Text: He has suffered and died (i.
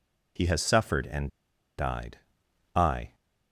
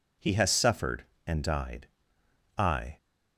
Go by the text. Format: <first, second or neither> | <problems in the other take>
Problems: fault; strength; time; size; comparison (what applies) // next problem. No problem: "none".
second | pauses between "and" and "died"; noticeable; at 1.3 s; 0.48 s long